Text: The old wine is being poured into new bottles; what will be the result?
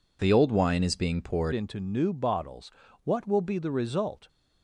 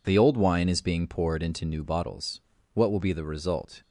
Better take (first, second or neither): second